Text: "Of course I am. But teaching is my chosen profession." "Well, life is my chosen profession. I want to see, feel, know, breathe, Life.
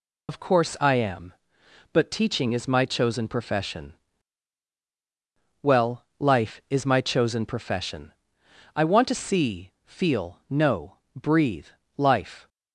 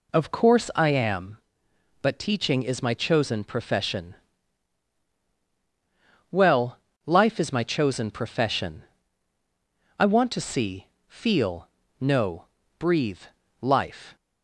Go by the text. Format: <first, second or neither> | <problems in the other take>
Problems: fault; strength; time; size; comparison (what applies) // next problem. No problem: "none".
second | loses the start of "Of"; at 0.2 s; 105 ms